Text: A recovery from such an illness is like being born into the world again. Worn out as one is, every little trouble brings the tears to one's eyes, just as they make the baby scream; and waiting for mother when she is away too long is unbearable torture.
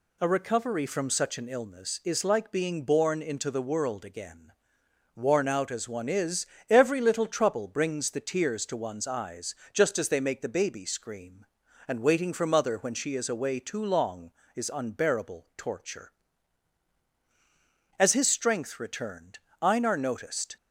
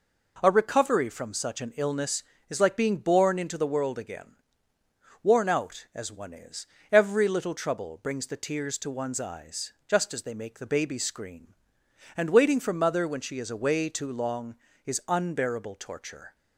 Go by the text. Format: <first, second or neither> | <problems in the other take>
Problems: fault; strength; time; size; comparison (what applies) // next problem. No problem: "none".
second | goes on to say "As his strength returned Einar noticed"; strong; from 17.9 s on; 2.6 s long